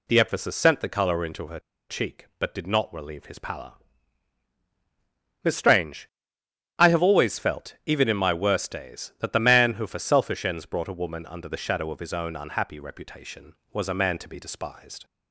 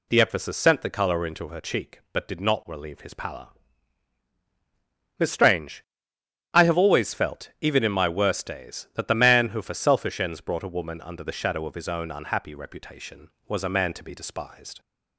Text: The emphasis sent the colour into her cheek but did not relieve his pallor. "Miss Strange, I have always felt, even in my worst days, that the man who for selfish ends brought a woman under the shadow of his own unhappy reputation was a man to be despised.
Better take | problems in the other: second | pauses between "her" and "cheek"; slight; at 1.5 s; 0.30 s long

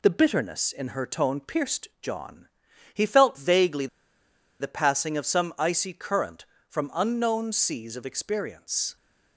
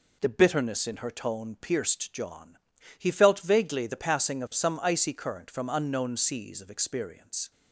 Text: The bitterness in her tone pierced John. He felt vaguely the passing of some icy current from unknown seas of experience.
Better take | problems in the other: second | pauses between "vaguely" and "the"; noticeable; at 3.8 s; 0.73 s long

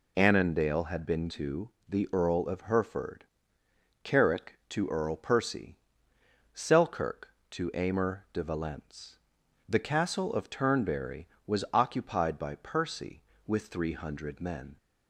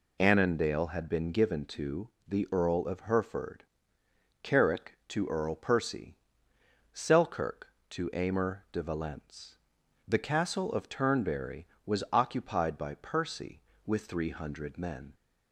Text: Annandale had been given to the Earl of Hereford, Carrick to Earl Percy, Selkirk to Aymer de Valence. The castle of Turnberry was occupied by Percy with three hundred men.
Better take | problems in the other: second | skips "given"; at 1.2 s // pauses between "to" and "the"; slight; at 1.7 s; 0.18 s long; slight in the second

